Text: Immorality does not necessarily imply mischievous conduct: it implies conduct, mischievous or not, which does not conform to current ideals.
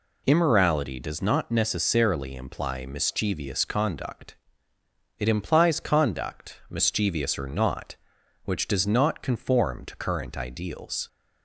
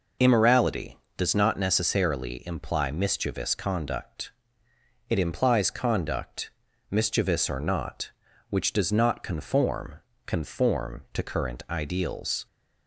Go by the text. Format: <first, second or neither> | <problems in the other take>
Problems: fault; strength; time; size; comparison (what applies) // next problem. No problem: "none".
first | says "conform" twice; at 10.2 s